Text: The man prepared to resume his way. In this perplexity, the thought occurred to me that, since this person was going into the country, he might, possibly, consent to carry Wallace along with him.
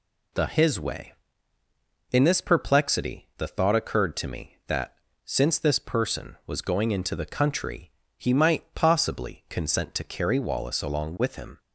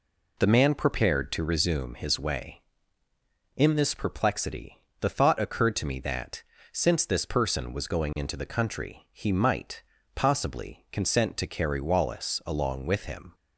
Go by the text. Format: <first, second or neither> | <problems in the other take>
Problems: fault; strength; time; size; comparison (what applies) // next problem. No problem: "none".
second | skips "man prepared to resume"; at 0.4 s